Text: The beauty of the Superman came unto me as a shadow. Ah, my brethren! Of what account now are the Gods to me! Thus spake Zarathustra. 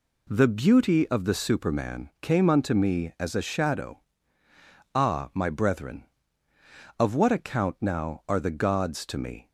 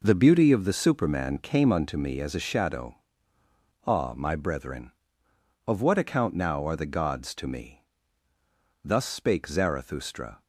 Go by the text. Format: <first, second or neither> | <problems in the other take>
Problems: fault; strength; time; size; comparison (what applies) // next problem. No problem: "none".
second | stops before "Thus spake Zarathustra"; at 9.4 s